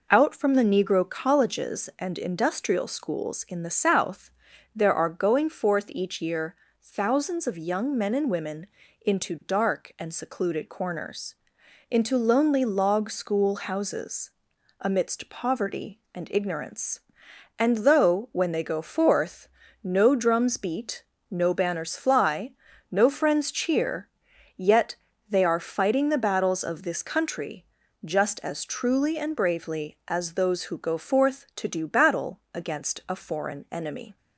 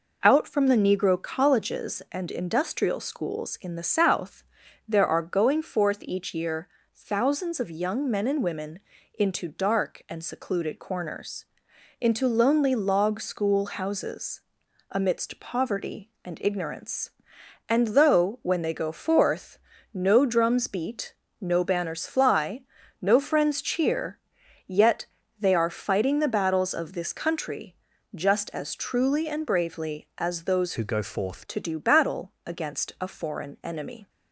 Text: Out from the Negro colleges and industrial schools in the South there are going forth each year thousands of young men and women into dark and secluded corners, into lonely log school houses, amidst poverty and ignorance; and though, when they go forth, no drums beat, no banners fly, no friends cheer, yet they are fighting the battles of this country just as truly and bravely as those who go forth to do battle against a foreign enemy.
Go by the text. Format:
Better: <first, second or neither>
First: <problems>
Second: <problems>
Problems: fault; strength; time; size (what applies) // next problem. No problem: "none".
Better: first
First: pauses between "South" and "there"; noticeable; at 4.3 s; 0.46 s long // pauses between "year" and "thousands"; slight; at 6.5 s; 0.28 s long // pauses between "women" and "into"; slight; at 8.6 s; 0.34 s long // pauses between "yet" and "they"; slight; at 24.9 s; 0.34 s long // pauses between "country" and "just"; at 27.6 s; 0.40 s long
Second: pauses between "South" and "there"; noticeable; at 4.4 s; 0.46 s long // pauses between "year" and "thousands"; slight; at 6.6 s; 0.28 s long // pauses between "women" and "into"; slight; at 8.7 s; 0.34 s long // pauses between "yet" and "they"; slight; at 25.0 s; 0.34 s long // pauses between "country" and "just"; at 27.7 s; 0.40 s long // changes voice from "who" to "forth"; from 30.7 to 31.4 s; 0.7 s long